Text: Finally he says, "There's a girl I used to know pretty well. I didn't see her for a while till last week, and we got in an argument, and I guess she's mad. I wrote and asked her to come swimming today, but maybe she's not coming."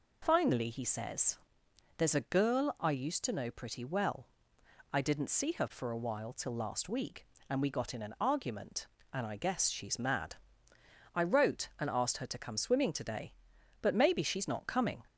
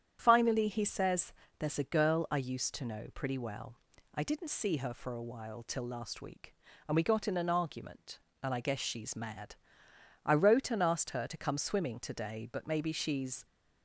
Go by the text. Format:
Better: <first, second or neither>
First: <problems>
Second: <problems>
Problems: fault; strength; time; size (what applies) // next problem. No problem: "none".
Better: first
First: none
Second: starts louder than the rest; strong; until 1.2 s; 9 dB // stops before "not coming"; at 13.4 s